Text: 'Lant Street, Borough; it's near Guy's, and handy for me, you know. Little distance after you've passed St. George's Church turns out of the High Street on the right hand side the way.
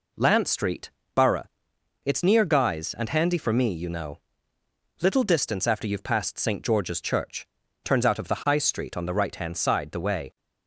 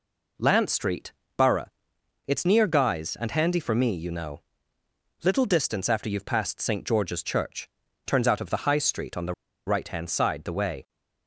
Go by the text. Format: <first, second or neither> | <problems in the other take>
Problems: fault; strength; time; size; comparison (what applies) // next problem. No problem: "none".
first | pauses between "Church" and "turns"; slight; at 7.6 s; 0.36 s long; slight in the first // pauses between "the" and "right"; slight; at 9.3 s; 0.33 s long